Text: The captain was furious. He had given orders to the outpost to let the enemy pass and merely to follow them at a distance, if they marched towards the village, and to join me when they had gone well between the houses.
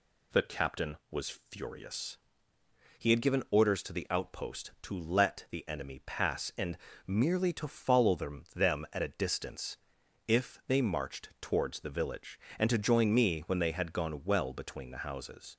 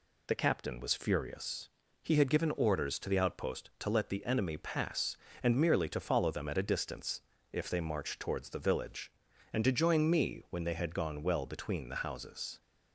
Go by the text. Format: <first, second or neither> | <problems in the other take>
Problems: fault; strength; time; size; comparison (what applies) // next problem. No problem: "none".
second | pauses between "and" and "merely"; slight; at 6.7 s; 0.30 s long // says "them" twice; at 8.5 s